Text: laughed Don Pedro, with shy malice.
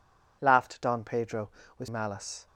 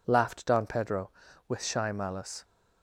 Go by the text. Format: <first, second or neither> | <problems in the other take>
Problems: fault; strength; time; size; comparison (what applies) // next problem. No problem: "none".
second | skips "shy"; at 1.8 s